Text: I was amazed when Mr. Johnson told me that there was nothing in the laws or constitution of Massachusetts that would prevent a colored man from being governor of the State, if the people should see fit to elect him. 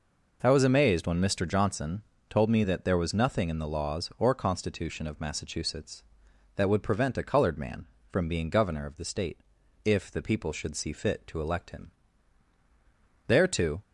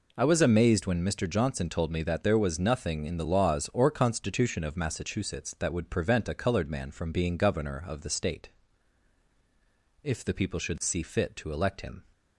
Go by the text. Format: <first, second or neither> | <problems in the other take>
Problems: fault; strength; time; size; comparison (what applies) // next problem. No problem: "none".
second | pauses between "Johnson" and "told"; slight; at 2.0 s; 0.30 s long // goes on to say "There too"; from 13.2 s on; 0.54 s long